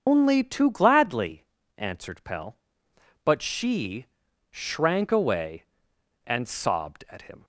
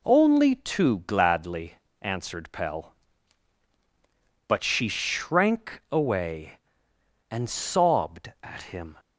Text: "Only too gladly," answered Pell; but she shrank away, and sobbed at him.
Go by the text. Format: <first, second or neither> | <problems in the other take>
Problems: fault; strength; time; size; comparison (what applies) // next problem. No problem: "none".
second | loses the start of "Only"; at 0.0 s; 135 ms // starts louder than the rest; until 1.0 s; 7 dB // pauses between "she" and "shrank"; at 4.0 s; 0.44 s long